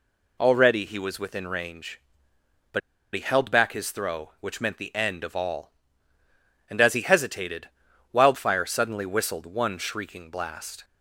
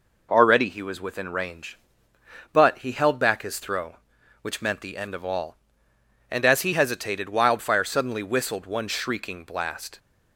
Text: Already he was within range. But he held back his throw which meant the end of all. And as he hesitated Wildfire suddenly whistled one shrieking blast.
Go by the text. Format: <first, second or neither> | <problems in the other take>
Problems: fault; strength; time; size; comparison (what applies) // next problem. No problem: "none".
second | pauses between "But" and "he"; slight; at 2.8 s; 0.33 s long // pauses between "hesitated" and "Wildfire"; at 7.6 s; 0.44 s long